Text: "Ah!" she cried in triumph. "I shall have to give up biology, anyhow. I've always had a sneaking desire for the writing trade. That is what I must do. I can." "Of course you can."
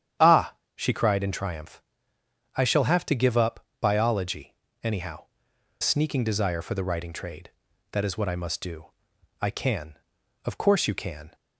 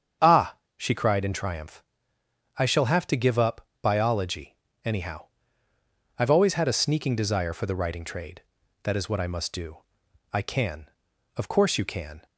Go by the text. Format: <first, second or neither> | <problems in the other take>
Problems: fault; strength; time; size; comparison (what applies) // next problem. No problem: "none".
second | starts louder than the rest; strong; until 1.4 s; 9.5 dB; strong in the second // pauses between "up" and "biology"; slight; at 3.6 s; 0.16 s long; slight in the second // skips "I've always had a"; at 5.5 s